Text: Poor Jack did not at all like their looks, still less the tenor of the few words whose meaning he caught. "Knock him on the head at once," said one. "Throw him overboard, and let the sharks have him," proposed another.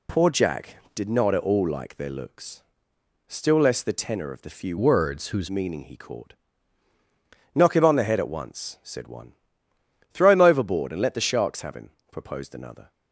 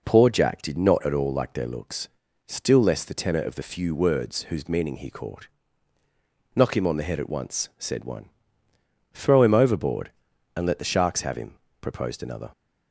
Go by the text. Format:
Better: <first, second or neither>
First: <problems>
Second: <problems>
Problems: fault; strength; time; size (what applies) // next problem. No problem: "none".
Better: second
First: changes voice from "words" to "whose"; from 4.7 to 5.4 s; 0.7 s long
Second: none